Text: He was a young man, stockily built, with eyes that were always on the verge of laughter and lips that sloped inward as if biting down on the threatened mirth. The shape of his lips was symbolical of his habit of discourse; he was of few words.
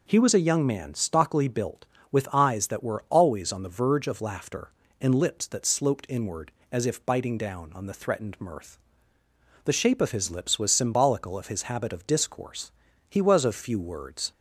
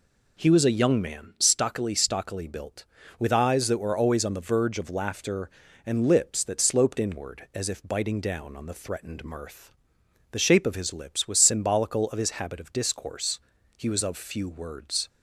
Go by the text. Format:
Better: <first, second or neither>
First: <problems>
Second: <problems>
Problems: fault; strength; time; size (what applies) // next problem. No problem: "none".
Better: first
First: none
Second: says "stockily" twice; at 1.9 s